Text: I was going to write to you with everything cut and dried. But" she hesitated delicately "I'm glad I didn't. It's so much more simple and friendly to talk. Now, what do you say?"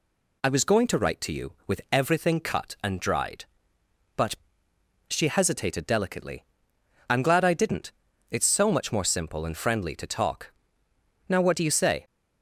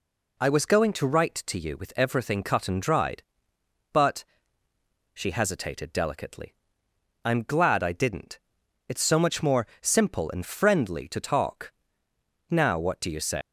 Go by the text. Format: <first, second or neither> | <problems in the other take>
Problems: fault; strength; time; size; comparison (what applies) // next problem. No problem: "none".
first | pauses between "But" and "she"; noticeable; at 4.2 s; 0.88 s long; noticeable in the first // pauses between "delicately" and "I'm"; noticeable; at 6.5 s; 0.70 s long; noticeable in the first // pauses between "more" and "simple"; slight; at 9.6 s; 0.16 s long // leaves "say" unfinished; at 13.4 s; 140 ms